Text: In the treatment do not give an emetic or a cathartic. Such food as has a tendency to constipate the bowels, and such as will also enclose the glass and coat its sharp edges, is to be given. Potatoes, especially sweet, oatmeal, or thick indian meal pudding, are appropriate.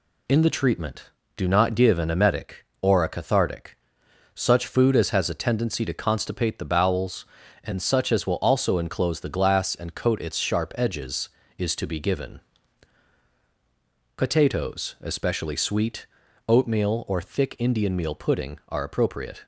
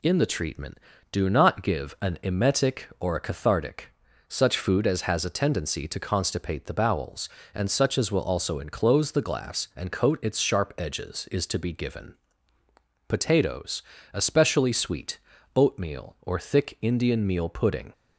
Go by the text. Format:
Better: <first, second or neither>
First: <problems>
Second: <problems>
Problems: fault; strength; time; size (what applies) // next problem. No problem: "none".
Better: first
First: none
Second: stops before "are appropriate"; at 17.9 s